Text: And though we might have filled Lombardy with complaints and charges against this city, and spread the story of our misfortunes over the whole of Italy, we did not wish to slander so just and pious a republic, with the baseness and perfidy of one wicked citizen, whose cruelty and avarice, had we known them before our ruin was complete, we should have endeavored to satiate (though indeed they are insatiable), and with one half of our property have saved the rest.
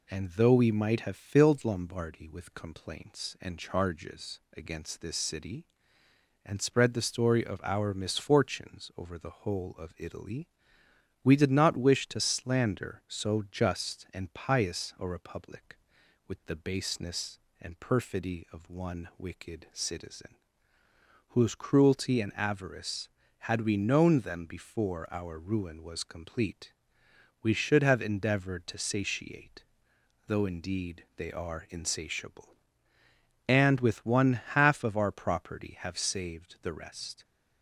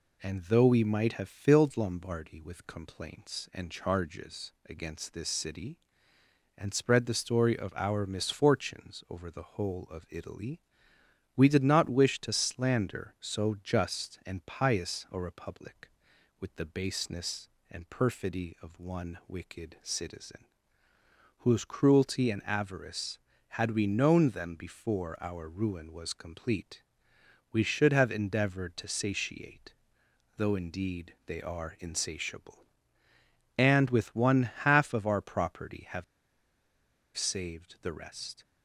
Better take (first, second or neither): first